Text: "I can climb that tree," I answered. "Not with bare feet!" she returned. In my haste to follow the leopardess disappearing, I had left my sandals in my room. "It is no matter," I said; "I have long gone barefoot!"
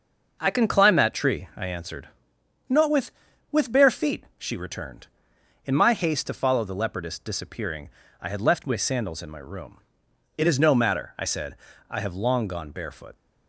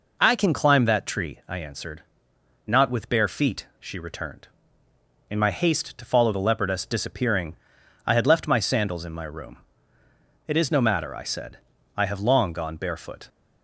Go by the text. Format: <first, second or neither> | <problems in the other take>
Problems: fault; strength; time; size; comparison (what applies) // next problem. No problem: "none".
second | says "with" twice; at 3.4 s